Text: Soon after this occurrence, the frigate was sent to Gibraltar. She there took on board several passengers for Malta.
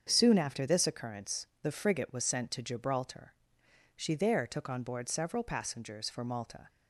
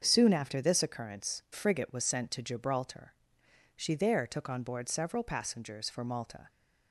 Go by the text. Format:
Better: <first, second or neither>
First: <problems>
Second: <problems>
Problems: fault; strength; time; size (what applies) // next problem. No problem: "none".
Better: first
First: starts louder than the rest; until 1.1 s; 7 dB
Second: starts louder than the rest; until 1.0 s; 7 dB // skips "the"; at 1.4 s